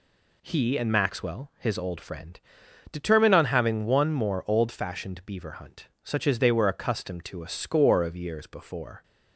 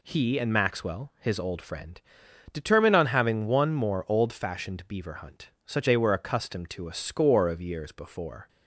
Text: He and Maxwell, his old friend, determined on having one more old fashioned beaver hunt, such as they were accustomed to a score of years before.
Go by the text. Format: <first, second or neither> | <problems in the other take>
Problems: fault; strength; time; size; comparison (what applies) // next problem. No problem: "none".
first | skips "as"; at 5.8 s